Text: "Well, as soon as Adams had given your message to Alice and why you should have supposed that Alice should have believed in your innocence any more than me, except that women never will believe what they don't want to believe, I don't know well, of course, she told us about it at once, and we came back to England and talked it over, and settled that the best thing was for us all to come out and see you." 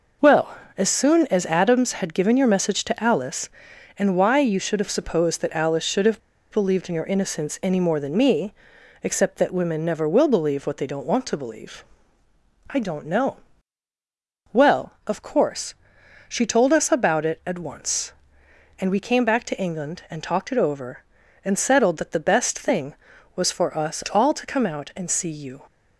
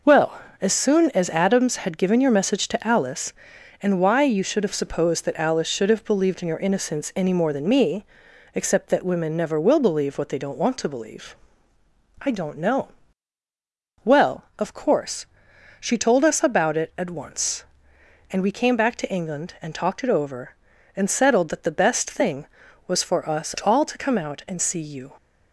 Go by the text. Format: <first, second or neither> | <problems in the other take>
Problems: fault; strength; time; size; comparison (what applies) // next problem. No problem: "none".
second | pauses between "have" and "believed"; slight; at 6.2 s; 0.31 s long // pauses between "know" and "well"; at 13.3 s; 1.1 s long; also in the second